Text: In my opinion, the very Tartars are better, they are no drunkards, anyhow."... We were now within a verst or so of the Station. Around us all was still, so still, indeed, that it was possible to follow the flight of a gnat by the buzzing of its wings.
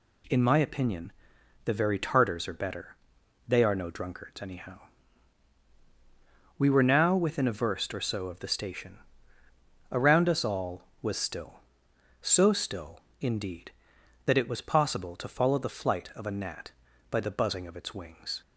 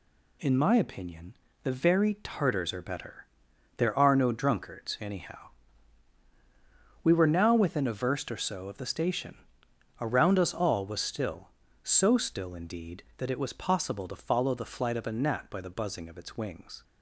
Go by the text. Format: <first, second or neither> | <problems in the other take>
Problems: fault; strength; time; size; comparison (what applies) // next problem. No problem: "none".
first | says "there" for "they"; at 3.7 s